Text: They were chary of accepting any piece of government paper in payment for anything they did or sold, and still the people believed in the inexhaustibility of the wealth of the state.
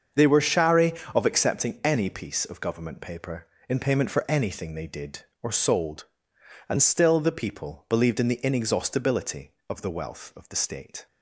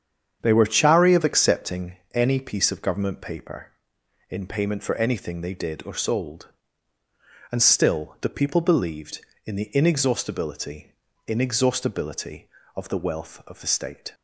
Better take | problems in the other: first | starts louder than the rest; strong; until 1.4 s; 8 dB; also in the first // pauses between "accepting" and "any"; slight; at 1.9 s; 0.18 s long // says "inexhaustibility" twice; at 11.2 s

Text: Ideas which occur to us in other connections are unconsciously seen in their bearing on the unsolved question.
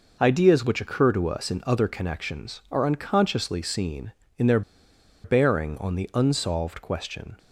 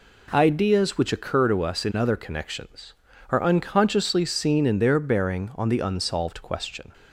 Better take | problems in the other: second | pauses between "their" and "bearing"; noticeable; at 4.6 s; 0.63 s long

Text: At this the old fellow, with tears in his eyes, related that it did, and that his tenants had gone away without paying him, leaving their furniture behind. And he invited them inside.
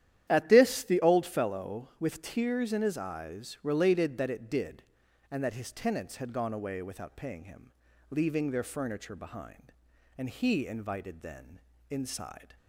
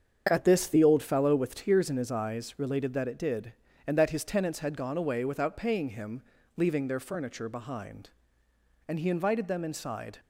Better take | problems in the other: second | starts louder than the rest; strong; until 1.3 s; 11 dB; strong in the second // says "then" for "them"; at 11.2 s

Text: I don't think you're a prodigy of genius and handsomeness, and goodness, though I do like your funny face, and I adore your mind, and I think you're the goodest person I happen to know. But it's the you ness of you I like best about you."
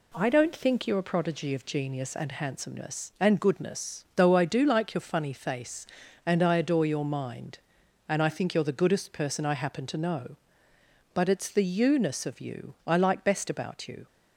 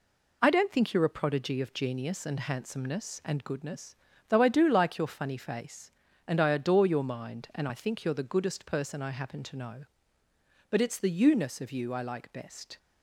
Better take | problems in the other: first | stops before "about you"; at 12.7 s

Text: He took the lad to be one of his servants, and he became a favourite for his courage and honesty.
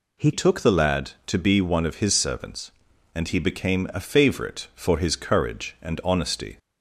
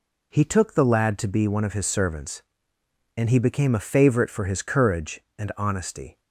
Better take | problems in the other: second | changes voice at "took"; from 0.3 s on; 6.2 s long

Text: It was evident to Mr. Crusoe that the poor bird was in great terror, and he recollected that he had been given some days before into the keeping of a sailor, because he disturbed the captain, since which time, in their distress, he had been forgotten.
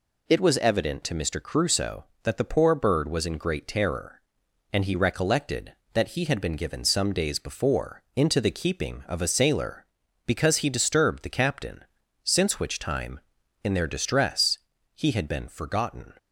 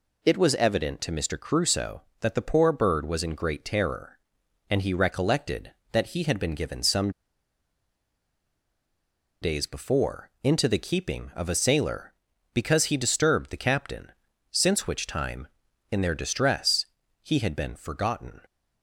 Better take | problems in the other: first | pauses between "some" and "days"; strong; at 7.0 s; 2.3 s long

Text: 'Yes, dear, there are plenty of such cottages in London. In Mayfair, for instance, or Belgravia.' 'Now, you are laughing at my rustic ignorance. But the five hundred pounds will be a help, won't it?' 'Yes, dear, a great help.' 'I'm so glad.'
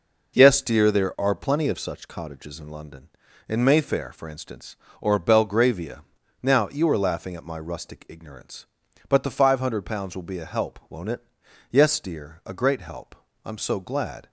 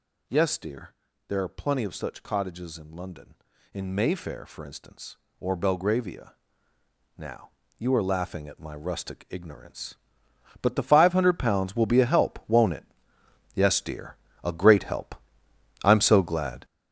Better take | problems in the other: first | gets louder; strong; throughout; 9.5 dB

